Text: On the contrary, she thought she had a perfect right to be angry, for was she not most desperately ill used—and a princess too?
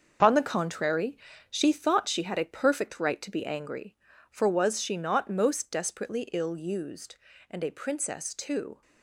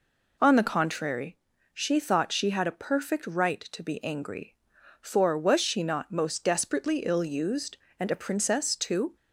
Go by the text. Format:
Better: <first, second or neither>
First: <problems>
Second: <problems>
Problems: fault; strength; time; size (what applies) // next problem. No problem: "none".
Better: second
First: gets quieter; strong; throughout; 9 dB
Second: none